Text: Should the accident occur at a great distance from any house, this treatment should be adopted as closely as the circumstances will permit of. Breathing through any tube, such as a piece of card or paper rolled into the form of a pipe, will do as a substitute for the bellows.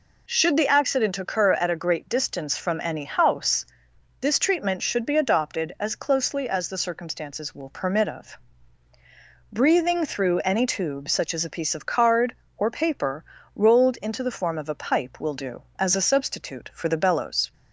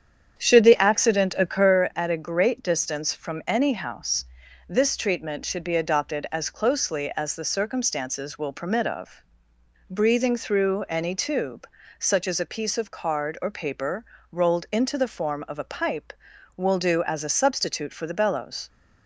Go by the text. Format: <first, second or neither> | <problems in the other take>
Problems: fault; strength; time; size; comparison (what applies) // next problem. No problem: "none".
first | starts louder than the rest; strong; until 1.8 s; 8.5 dB // pauses between "paper" and "rolled"; slight; at 14.0 s; 0.26 s long; slight in the first